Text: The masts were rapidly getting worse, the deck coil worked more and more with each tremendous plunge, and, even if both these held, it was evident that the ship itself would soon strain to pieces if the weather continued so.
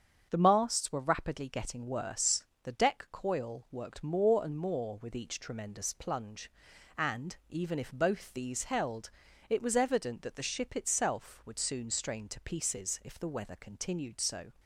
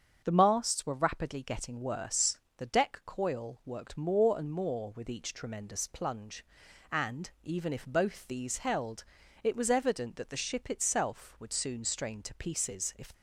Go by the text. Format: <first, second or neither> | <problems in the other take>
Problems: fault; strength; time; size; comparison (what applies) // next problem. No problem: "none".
first | starts louder than the rest; strong; until 1.2 s; 7.5 dB; strong in the first // stops before "the weather continued so"; at 13.1 s